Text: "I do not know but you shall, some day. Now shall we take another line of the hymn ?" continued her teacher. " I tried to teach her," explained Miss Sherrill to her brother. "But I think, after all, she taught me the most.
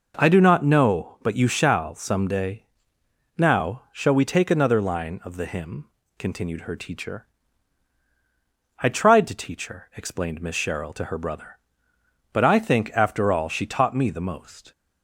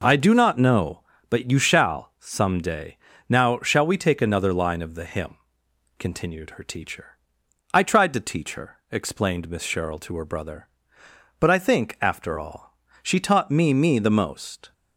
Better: first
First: none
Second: says "me" twice; at 13.7 s

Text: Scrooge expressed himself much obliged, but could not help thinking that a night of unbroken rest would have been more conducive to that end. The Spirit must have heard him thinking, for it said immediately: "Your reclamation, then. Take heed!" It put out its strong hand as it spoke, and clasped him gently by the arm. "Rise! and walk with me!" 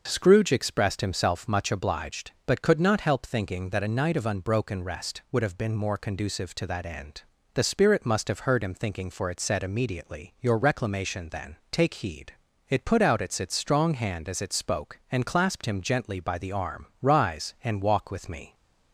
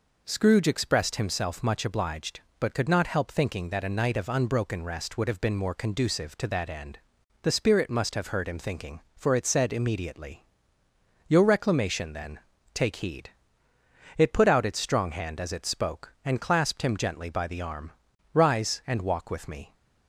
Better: second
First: says "its" twice; at 13.4 s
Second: none

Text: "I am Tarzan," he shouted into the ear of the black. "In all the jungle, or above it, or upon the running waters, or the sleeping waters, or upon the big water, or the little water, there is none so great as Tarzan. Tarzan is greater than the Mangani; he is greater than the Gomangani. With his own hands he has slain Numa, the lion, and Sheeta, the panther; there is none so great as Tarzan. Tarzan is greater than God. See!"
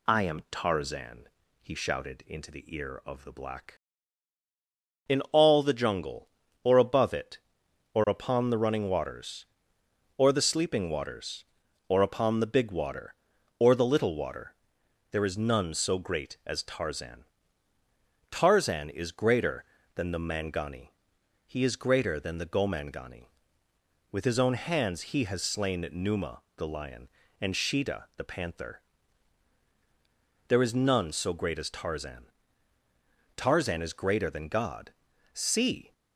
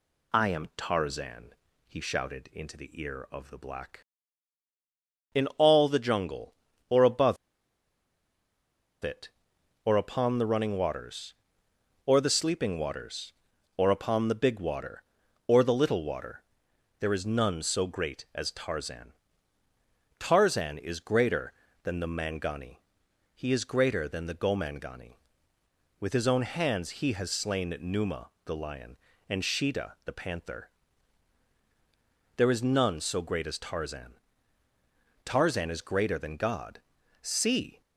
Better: first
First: none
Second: pauses between "above" and "it"; strong; at 7.3 s; 1.6 s long

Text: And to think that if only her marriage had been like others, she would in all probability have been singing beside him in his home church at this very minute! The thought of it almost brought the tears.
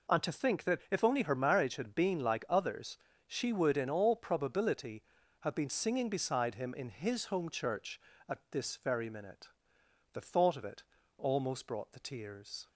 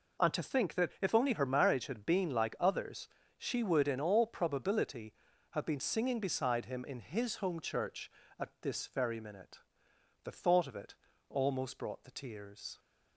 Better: neither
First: pauses between "it" and "almost"; slight; at 10.8 s; 0.34 s long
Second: pauses between "it" and "almost"; slight; at 10.9 s; 0.34 s long

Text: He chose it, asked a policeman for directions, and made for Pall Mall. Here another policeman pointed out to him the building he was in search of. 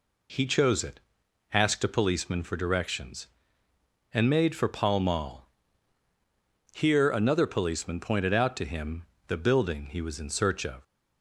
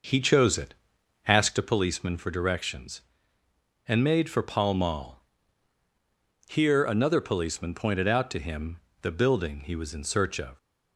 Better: first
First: pauses between "him" and "the"; slight; at 9.0 s; 0.24 s long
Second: starts louder than the rest; noticeable; until 1.6 s; 6 dB // pauses between "him" and "the"; slight; at 8.7 s; 0.24 s long

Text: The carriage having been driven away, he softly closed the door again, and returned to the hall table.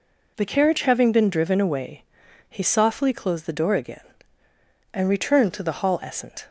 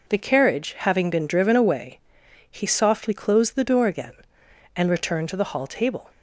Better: second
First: says "essent" for "table"; at 6.0 s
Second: none

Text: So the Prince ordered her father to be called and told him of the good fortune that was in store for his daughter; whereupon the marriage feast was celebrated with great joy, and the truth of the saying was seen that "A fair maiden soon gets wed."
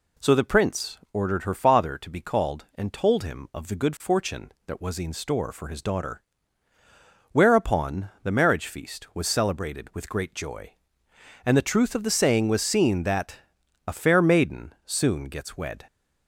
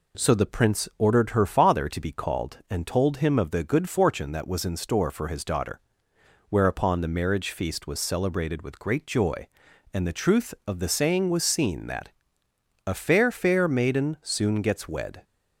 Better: first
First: pauses between "that" and "A"; noticeable; at 13.3 s; 0.50 s long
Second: pauses between "that" and "A"; noticeable; at 12.0 s; 0.76 s long // says "fair" twice; at 13.3 s

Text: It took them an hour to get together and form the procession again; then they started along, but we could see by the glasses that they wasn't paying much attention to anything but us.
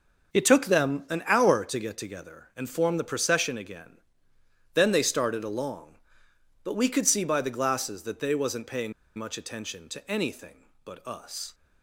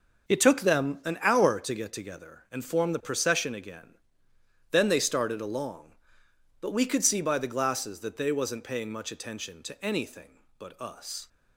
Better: second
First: starts louder than the rest; until 1.4 s; 6.5 dB // pauses between "paying" and "much"; slight; at 8.9 s; 0.25 s long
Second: starts louder than the rest; until 1.3 s; 6.5 dB

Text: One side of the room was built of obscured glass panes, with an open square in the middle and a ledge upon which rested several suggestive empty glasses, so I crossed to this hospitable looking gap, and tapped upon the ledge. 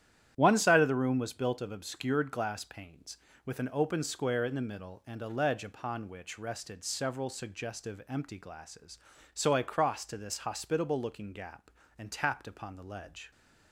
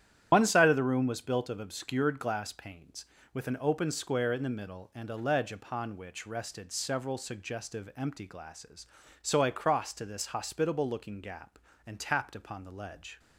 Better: first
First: starts louder than the rest; strong; until 1.3 s; 11 dB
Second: loses the start of "One"; at 0.3 s; 75 ms // starts louder than the rest; strong; until 1.3 s; 10.5 dB

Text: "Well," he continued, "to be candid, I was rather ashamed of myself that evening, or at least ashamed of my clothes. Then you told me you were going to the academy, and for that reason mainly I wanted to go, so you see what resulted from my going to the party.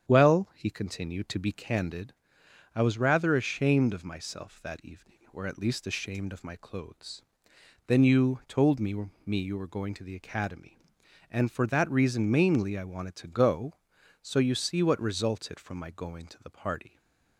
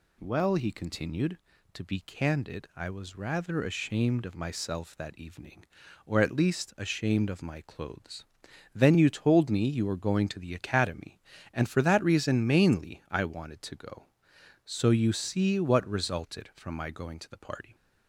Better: second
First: starts louder than the rest; strong; until 1.1 s; 8.5 dB // says "me" twice; at 9.2 s // stays silent after the last word; slight; from 16.8 s on; 0.5 s long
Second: none

